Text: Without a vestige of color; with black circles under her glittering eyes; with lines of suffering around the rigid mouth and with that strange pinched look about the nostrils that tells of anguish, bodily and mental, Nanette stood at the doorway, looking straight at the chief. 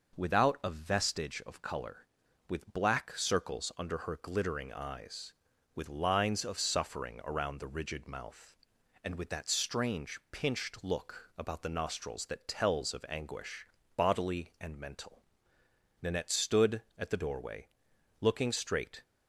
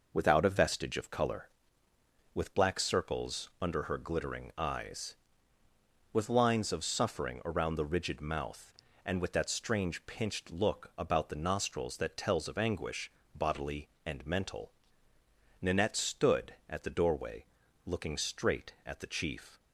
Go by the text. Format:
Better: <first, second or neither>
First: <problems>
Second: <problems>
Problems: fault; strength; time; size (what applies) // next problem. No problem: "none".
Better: second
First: stops before "at the chief"; at 19.0 s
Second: none